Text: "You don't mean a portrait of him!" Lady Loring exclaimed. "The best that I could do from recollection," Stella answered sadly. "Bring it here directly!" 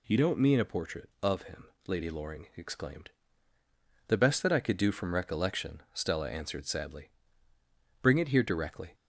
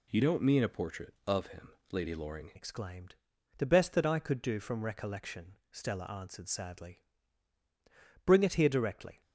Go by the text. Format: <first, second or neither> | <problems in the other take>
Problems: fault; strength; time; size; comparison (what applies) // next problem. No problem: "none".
first | changes voice at "exclaimed"; from 2.5 s on; 6.7 s long